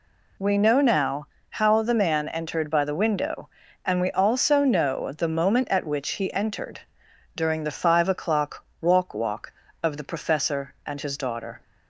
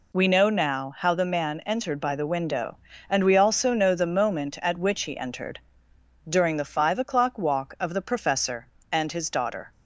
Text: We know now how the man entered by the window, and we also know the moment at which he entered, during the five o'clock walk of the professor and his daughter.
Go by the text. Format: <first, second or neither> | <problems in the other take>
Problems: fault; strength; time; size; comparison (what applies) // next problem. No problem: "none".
second | pauses between "now" and "how"; slight; at 1.2 s; 0.24 s long // pauses between "o'clock" and "walk"; slight; at 8.6 s; 0.16 s long // says "walk" twice; at 9.1 s